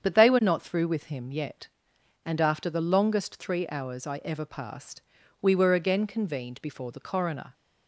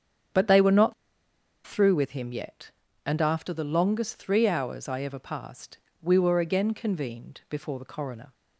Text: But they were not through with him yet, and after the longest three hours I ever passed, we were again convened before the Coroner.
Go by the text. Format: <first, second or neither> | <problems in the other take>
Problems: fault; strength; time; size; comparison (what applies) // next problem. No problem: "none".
first | starts louder than the rest; strong; until 2.0 s; 8 dB; strong in the first // pauses between "not" and "through"; noticeable; at 0.9 s; 0.73 s long